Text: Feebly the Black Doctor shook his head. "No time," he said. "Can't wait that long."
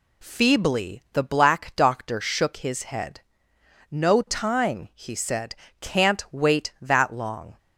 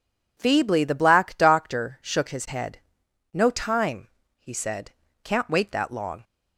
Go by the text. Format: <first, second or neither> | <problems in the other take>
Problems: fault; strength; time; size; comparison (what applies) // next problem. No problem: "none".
neither | none